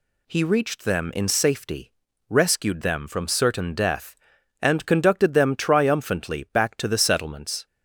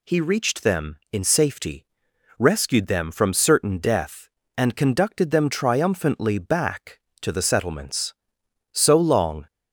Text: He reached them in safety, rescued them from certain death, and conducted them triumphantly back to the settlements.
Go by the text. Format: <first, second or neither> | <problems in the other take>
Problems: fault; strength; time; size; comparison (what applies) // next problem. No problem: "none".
first | goes on to say "So long"; noticeable; from 8.7 s on; 0.76 s long